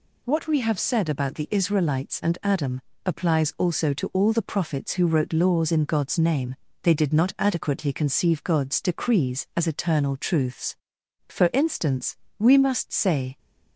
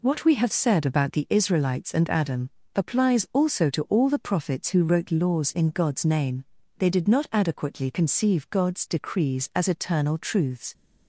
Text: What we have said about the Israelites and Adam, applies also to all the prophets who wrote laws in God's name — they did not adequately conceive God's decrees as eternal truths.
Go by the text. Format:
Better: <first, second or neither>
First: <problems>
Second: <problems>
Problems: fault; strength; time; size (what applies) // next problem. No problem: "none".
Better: second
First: goes on to say "For instance we must say"; strong; from 11.2 s on; 2.1 s long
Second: none